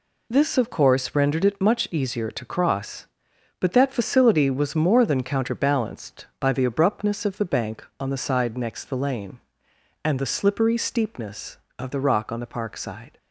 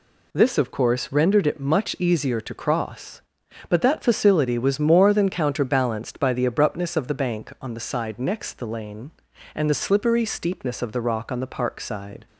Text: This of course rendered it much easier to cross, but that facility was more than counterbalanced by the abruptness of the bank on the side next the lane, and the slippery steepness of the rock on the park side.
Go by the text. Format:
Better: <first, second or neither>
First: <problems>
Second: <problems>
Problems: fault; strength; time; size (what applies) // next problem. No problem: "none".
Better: neither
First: none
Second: none